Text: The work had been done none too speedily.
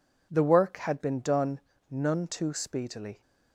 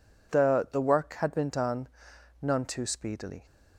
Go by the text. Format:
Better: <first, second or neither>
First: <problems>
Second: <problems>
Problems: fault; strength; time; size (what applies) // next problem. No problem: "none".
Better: first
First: pauses between "done" and "none"; slight; at 1.6 s; 0.30 s long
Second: says "The" twice; at 0.6 s // pauses between "done" and "none"; noticeable; at 1.8 s; 0.52 s long